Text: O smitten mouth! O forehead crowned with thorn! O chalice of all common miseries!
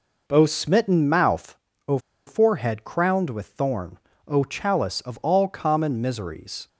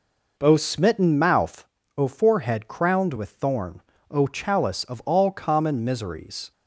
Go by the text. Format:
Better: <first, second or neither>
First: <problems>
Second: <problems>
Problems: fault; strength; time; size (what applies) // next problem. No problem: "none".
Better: second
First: pauses between "O" and "forehead"; slight; at 1.9 s; 0.28 s long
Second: none